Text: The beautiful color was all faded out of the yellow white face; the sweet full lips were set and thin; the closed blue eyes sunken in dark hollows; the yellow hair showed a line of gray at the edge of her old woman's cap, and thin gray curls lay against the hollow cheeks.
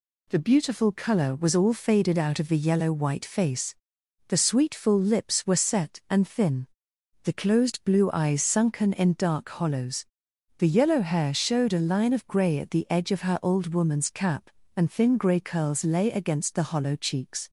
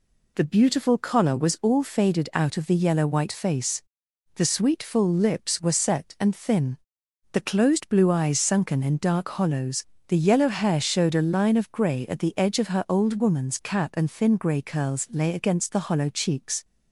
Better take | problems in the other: first | says "collar" for "color"; at 0.9 s

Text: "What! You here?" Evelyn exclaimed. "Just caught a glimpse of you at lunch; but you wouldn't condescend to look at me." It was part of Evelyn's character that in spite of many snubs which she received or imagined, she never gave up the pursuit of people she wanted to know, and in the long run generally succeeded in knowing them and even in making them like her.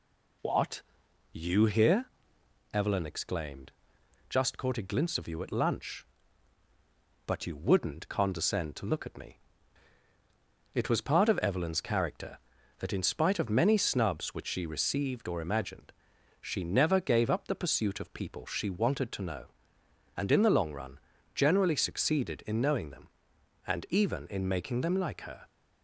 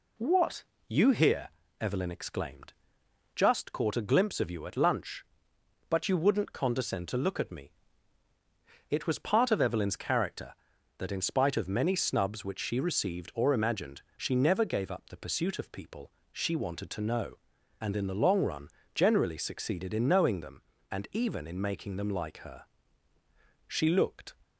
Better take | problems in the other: first | pauses between "people" and "she"; slight; at 16.1 s; 0.18 s long // pauses between "run" and "generally"; slight; at 18.6 s; 0.26 s long; slight in the first // goes on to say "She looked"; noticeable; from 23.6 s on; 0.68 s long

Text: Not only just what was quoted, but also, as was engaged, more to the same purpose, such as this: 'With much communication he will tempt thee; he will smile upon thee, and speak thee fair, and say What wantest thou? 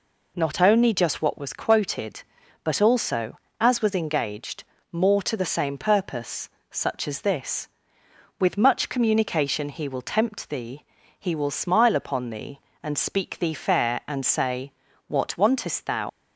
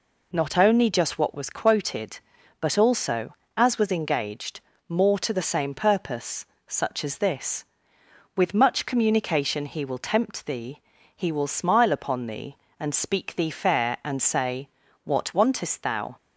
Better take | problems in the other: second | pauses between "say" and "What"; slight; at 14.7 s; 0.34 s long; slight in the second // leaves "thou" unfinished; at 16.0 s; 95 ms

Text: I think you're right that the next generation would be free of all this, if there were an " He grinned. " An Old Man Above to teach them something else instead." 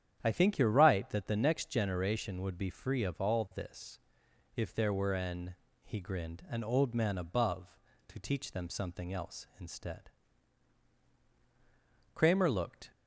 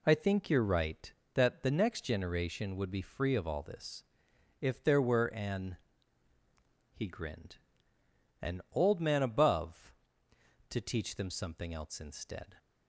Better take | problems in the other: second | starts louder than the rest; strong; until 1.2 s; 9.5 dB // goes on to say "Kramer looked"; noticeable; from 12.1 s on; 0.78 s long

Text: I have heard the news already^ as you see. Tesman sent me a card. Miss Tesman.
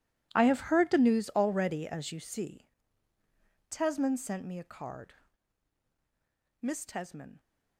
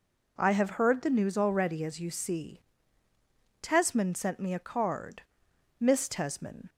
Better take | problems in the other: second | gets quieter; strong; throughout; 17.5 dB

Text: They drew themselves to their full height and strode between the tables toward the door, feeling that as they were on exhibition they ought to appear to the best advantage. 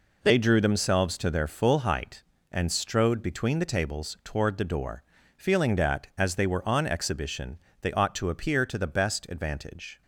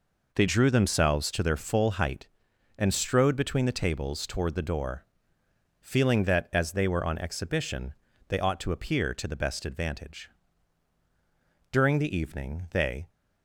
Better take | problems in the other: first | pauses between "exhibition" and "they"; slight; at 7.9 s; 0.34 s long; slight in the first // goes on to say "During the evening they"; from 11.7 s on; 1.3 s long

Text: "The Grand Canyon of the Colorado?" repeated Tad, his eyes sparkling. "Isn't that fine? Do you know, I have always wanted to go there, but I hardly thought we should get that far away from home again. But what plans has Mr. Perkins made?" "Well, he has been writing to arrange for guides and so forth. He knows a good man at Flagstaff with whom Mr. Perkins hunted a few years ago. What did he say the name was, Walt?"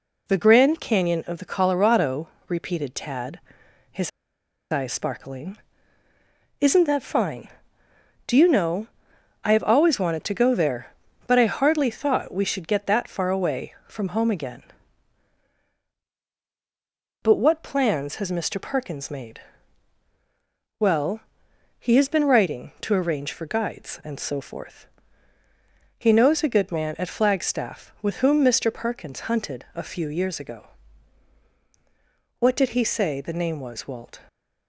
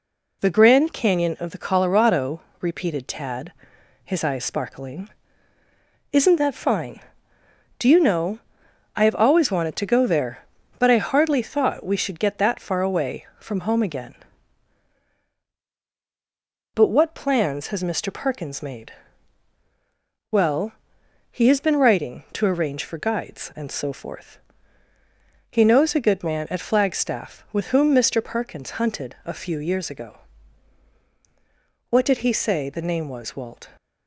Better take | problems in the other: second | pauses between "his" and "eyes"; noticeable; at 4.1 s; 0.61 s long

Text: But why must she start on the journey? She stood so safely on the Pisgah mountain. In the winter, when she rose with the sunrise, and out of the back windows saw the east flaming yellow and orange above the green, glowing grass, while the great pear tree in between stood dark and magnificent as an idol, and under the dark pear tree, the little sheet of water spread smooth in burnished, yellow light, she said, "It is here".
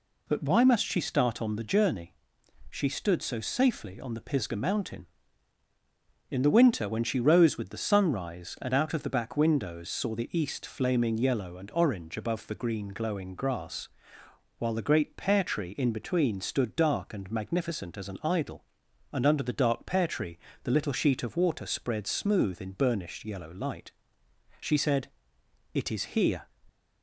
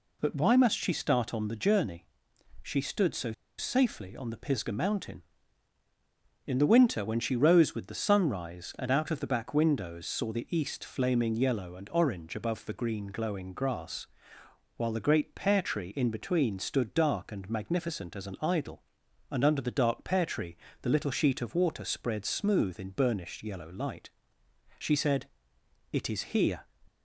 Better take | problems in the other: first | pauses between "so" and "safely"; slight; at 3.3 s; 0.26 s long

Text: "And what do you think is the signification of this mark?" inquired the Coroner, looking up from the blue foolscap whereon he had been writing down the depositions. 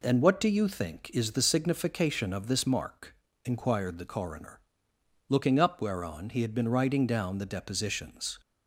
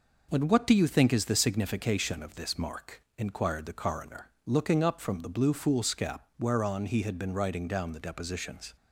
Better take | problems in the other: second | skips "from the blue foolscap"; at 5.8 s

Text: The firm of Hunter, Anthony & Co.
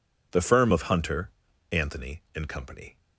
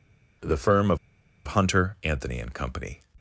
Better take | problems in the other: first | pauses between "of" and "Hunter"; noticeable; at 0.9 s; 0.50 s long

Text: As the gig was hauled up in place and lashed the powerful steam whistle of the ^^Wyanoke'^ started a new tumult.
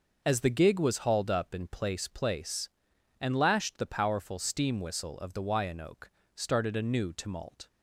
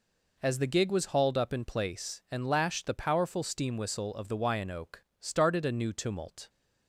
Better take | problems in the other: second | says "place" twice; at 2.0 s // pauses between "Wyanoke" and "started"; slight; at 6.1 s; 0.24 s long; slight in the second

